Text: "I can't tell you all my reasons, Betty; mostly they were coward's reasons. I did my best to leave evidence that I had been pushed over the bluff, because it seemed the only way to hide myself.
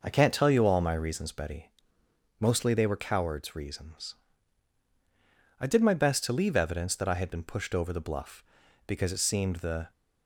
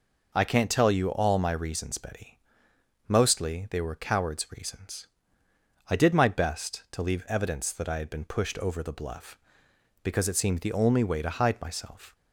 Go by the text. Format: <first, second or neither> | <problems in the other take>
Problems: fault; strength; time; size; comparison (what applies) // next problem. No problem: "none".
second | stops before "only way to hide myself"; at 9.9 s